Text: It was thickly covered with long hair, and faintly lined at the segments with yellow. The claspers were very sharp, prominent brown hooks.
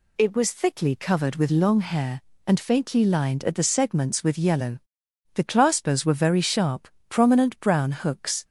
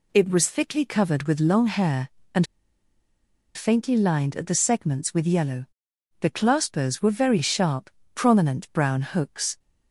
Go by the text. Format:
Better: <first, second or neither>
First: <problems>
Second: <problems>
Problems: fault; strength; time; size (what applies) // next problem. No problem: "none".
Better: first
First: none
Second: pauses between "and" and "faintly"; at 2.4 s; 1.1 s long